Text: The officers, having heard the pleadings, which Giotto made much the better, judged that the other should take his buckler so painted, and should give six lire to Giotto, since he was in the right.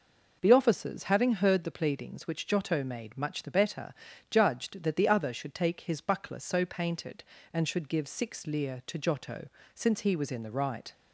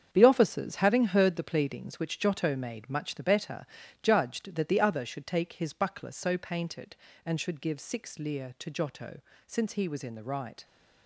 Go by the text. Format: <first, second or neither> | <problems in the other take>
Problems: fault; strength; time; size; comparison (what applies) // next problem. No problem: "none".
first | gets quieter; strong; throughout; 9.5 dB